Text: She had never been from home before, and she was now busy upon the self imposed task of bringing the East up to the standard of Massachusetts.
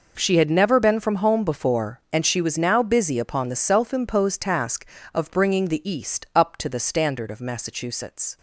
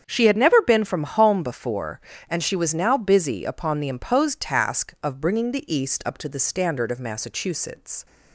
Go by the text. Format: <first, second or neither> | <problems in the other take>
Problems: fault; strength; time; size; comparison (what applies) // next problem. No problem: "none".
first | starts louder than the rest; strong; until 1.0 s; 8 dB // skips "self"; at 3.8 s